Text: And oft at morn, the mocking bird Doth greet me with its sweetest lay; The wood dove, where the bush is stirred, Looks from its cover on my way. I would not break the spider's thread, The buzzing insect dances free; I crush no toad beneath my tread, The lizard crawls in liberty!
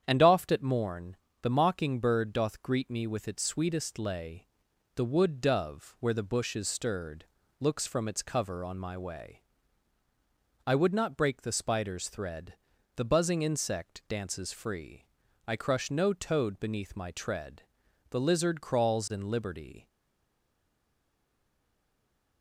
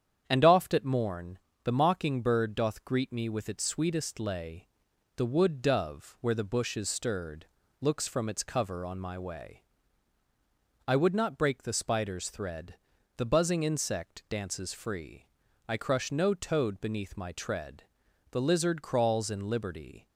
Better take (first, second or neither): second